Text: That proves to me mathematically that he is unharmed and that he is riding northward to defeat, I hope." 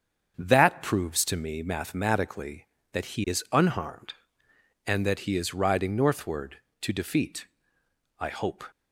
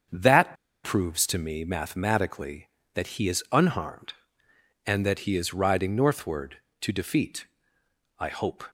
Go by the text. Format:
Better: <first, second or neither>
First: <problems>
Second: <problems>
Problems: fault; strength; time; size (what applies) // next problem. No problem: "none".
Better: first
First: starts louder than the rest; until 1.3 s; 7 dB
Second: starts louder than the rest; until 1.4 s; 7 dB // pauses between "That" and "proves"; slight; at 0.5 s; 0.28 s long